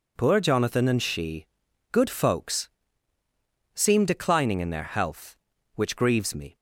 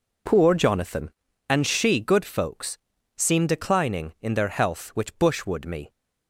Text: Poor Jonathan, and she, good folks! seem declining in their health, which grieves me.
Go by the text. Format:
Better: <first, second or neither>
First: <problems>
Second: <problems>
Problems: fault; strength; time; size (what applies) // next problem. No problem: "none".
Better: first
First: none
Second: says "bushwood" for "grieves"; at 5.1 s